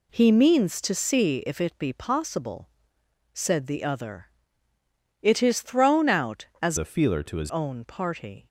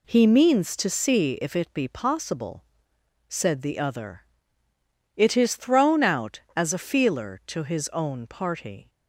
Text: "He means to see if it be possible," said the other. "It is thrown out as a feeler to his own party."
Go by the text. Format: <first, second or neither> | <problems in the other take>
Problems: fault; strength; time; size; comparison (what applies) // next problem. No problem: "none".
second | changes voice from "a" to "his"; from 6.7 to 7.4 s; 0.7 s long